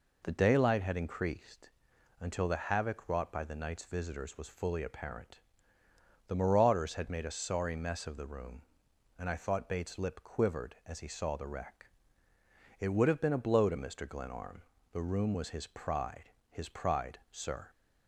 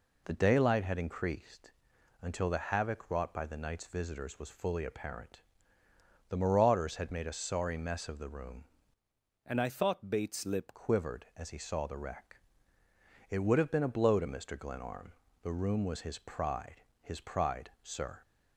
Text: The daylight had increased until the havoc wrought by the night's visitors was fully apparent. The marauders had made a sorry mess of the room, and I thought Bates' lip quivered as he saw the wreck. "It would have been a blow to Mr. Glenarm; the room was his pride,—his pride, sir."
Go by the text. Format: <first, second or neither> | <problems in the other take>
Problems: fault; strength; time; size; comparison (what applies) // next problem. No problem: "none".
first | pauses between "increased" and "until"; noticeable; at 1.7 s; 0.50 s long; noticeable in the first // changes voice from "and" to "lip"; from 9.4 to 10.7 s; 1.3 s long